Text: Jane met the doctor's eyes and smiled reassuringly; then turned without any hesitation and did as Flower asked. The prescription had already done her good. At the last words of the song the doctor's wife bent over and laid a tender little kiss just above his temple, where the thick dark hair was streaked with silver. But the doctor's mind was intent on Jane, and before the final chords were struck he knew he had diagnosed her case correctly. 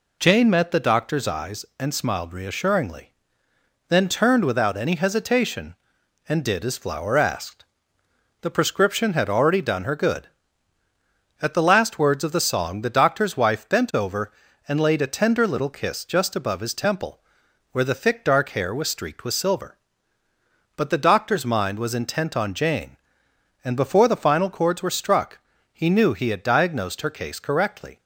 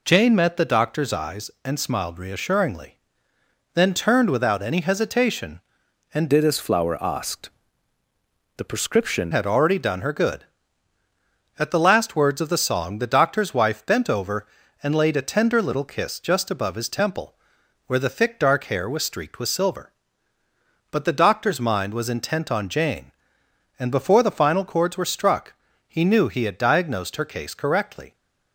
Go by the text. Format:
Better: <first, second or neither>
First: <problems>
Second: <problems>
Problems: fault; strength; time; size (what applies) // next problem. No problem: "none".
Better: first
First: pauses between "struck" and "he"; slight; at 25.3 s; 0.34 s long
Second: changes voice from "did" to "prescription"; from 6.3 to 9.3 s; 3.0 s long // pauses between "struck" and "he"; slight; at 25.5 s; 0.34 s long